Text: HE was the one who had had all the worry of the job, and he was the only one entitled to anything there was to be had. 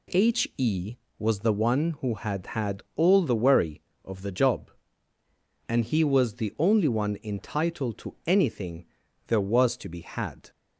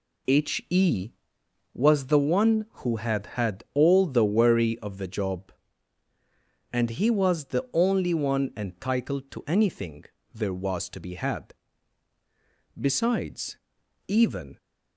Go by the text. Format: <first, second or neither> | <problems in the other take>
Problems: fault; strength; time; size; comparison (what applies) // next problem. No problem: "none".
first | pauses between "anything" and "there"; slight; at 10.0 s; 0.30 s long; also in the first // goes on to say "Besides even"; strong; from 12.7 s on; 1.7 s long